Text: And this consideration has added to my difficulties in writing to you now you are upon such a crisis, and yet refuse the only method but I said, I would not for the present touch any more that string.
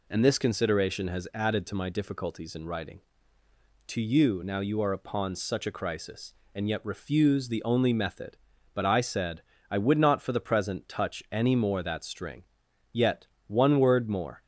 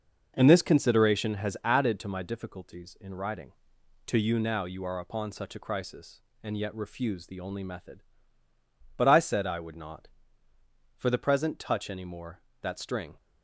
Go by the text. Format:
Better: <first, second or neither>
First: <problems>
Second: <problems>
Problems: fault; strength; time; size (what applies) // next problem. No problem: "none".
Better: second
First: goes on to say "Yet one word more"; from 12.9 s on; 1.4 s long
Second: none